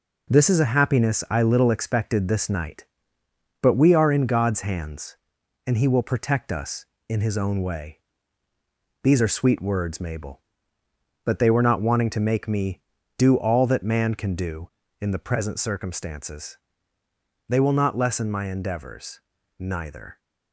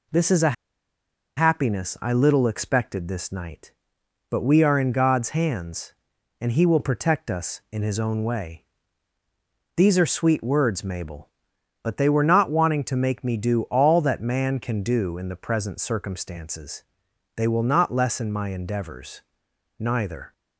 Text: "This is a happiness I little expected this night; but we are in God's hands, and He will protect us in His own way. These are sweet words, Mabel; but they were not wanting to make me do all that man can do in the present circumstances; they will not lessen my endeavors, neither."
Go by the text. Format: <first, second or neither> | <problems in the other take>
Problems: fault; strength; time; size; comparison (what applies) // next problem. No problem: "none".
first | pauses between "a" and "happiness"; noticeable; at 0.5 s; 0.83 s long